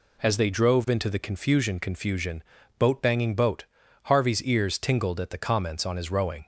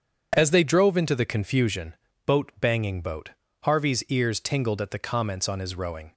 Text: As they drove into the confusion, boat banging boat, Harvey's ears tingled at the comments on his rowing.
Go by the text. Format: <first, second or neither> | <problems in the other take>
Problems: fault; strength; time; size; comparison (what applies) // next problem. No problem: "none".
second | says "confusion" twice; at 1.7 s